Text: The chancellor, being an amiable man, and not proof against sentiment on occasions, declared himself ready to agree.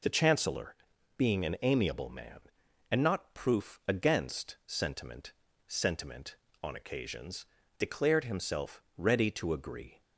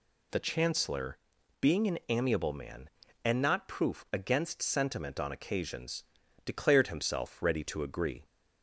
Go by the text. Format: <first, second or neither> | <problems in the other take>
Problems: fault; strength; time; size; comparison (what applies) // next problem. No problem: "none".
second | says "sentiment" twice; at 5.6 s // pauses between "himself" and "ready"; slight; at 8.8 s; 0.16 s long